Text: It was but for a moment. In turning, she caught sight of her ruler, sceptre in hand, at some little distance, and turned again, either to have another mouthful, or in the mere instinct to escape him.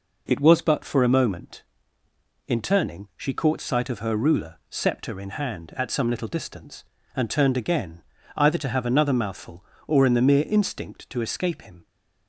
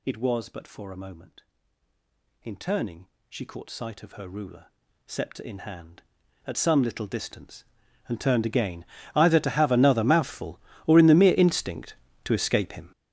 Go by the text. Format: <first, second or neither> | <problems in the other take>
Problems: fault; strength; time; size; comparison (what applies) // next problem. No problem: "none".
first | gets louder; strong; throughout; 14.5 dB